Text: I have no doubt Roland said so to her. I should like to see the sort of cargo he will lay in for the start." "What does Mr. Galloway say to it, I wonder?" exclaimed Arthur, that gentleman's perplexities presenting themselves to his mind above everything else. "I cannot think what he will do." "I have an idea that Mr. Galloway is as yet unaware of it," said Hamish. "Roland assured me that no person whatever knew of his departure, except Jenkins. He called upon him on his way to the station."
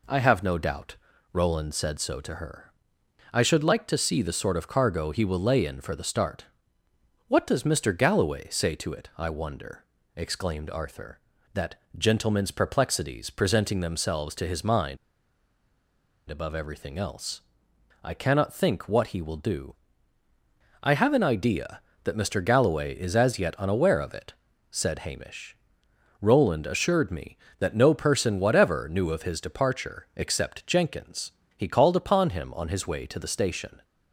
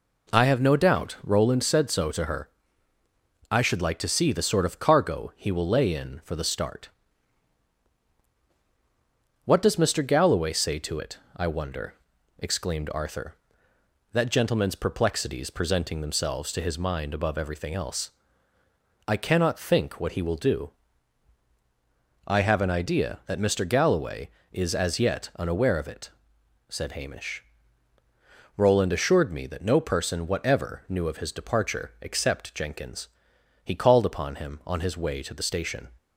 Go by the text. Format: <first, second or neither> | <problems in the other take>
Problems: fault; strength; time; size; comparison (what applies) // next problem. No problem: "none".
second | pauses between "doubt" and "Roland"; slight; at 0.9 s; 0.34 s long // pauses between "that" and "gentleman's"; slight; at 11.7 s; 0.22 s long // pauses between "mind" and "above"; strong; at 14.9 s; 1.3 s long